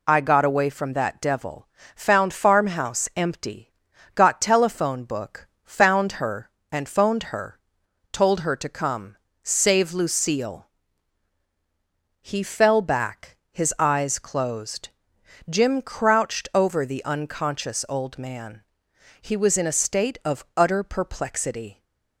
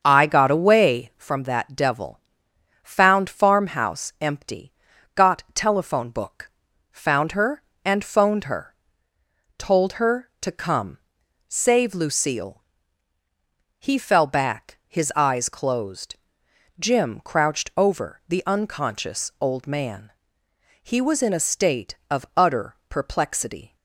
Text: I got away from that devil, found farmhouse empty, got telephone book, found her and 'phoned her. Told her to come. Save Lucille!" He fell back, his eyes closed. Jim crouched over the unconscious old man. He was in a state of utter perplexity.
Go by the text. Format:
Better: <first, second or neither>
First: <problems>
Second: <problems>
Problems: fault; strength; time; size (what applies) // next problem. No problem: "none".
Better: first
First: none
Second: starts louder than the rest; until 1.3 s; 6.5 dB